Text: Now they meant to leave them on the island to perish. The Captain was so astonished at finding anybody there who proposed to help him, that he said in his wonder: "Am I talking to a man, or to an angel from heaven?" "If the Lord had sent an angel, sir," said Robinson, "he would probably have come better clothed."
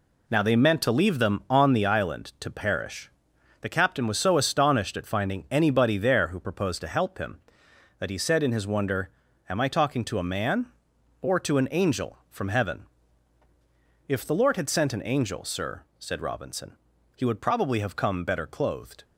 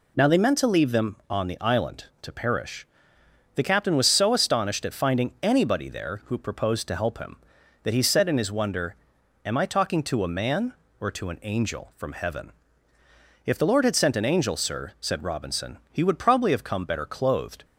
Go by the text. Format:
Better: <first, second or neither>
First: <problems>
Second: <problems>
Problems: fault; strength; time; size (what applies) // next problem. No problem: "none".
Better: neither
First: none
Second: none